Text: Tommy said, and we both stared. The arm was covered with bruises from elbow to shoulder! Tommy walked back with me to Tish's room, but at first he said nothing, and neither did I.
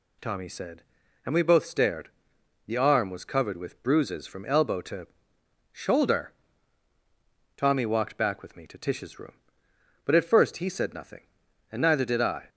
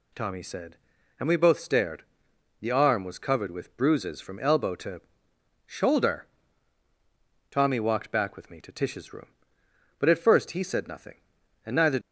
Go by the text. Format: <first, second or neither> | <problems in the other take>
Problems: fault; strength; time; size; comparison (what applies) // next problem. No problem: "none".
first | pauses between "to" and "shoulder"; noticeable; at 5.0 s; 0.64 s long; noticeable in the first // stops before "did I"; at 12.0 s